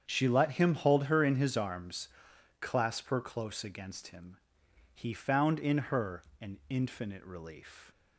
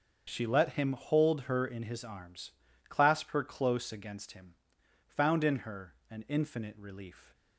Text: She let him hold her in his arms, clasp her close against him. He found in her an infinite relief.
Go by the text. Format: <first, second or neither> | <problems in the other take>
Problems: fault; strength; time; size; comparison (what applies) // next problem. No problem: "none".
first | starts louder than the rest; until 1.2 s; 7 dB; strong in the first // skips "He"; at 4.8 s // pauses between "her" and "an"; slight; at 5.9 s; 0.16 s long; slight in the first